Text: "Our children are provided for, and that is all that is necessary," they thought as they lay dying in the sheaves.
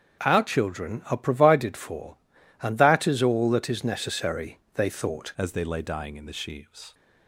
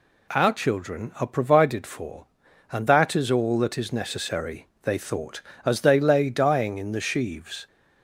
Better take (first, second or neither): second